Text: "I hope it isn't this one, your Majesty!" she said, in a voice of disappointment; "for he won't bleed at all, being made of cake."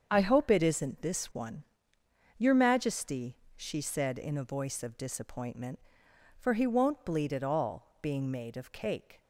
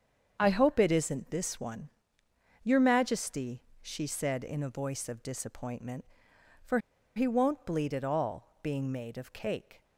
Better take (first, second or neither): first